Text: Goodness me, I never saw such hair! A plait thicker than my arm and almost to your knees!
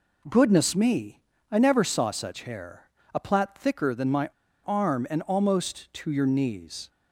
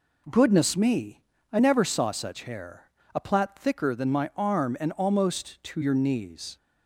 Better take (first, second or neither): second